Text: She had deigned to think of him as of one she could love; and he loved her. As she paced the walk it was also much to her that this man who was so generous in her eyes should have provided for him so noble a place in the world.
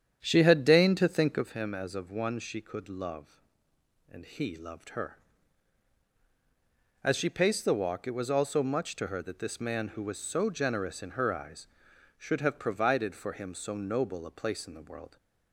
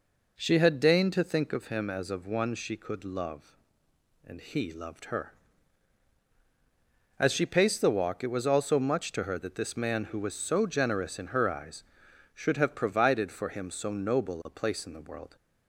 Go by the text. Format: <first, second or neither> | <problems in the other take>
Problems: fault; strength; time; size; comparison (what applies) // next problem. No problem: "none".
second | starts louder than the rest; strong; until 1.5 s; 9 dB